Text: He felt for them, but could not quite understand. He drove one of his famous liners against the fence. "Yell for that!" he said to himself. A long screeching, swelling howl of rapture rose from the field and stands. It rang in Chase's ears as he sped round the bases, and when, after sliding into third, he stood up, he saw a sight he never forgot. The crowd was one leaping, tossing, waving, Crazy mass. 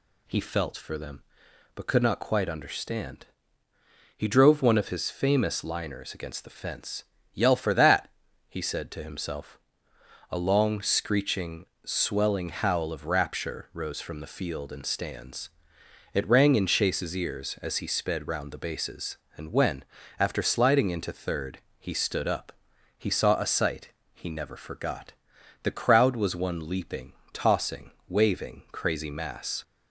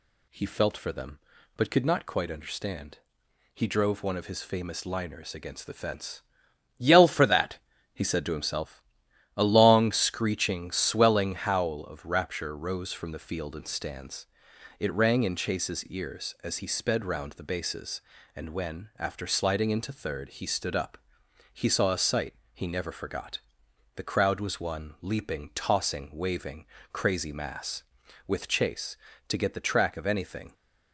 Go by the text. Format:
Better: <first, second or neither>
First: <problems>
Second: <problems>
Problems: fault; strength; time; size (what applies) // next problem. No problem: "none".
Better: first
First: pauses between "sight" and "he"; slight; at 23.9 s; 0.22 s long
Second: pauses between "sight" and "he"; slight; at 22.3 s; 0.18 s long // goes on to say "With Chase to get the track of anything"; strong; from 28.2 s on; 2.2 s long